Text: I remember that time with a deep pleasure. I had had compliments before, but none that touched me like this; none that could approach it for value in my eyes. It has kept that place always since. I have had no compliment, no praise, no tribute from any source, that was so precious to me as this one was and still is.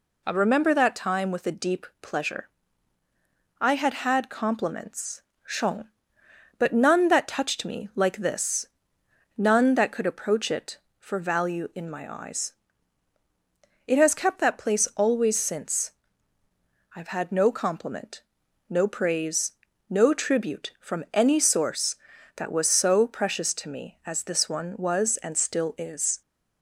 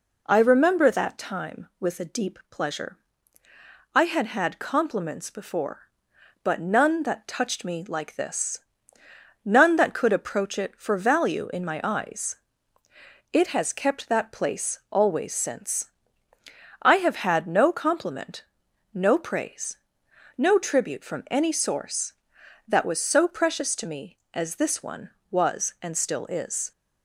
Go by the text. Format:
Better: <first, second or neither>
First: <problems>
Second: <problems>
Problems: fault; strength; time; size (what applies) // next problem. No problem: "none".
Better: second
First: says "shong" for "before"; at 5.4 s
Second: none